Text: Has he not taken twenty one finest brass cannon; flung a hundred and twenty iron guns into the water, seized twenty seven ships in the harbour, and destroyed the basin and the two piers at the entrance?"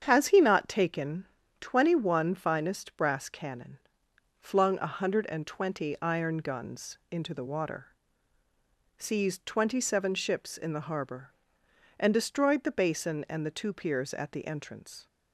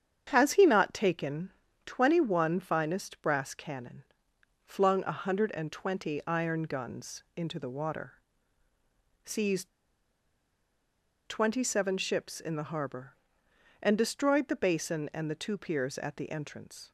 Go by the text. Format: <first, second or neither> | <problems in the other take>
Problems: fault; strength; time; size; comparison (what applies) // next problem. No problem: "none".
first | starts louder than the rest; strong; until 1.2 s; 8 dB; strong in the first // pauses between "taken" and "twenty"; slight; at 1.5 s; 0.34 s long; slight in the first // pauses between "seized" and "twenty"; strong; at 9.6 s; 1.5 s long